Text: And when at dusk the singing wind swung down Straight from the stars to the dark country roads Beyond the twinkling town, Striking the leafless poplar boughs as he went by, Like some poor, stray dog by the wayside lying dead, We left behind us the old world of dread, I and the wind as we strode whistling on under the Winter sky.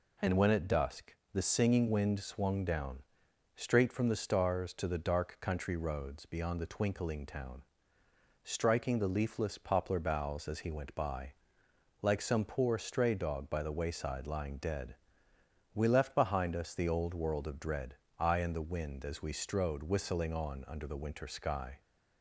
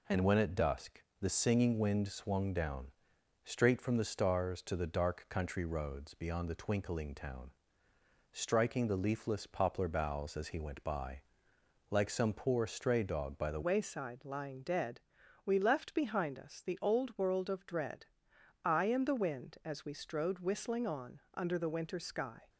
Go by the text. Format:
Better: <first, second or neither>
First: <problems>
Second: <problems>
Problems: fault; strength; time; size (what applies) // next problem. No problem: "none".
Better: first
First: pauses between "dusk" and "the"; slight; at 1.1 s; 0.18 s long // pauses between "down" and "Straight"; noticeable; at 3.0 s; 0.52 s long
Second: pauses between "dusk" and "the"; slight; at 1.0 s; 0.18 s long // pauses between "down" and "Straight"; noticeable; at 2.9 s; 0.52 s long // changes voice at "wayside"; from 13.6 s on; 8.8 s long // pauses between "on" and "under"; slight; at 21.1 s; 0.16 s long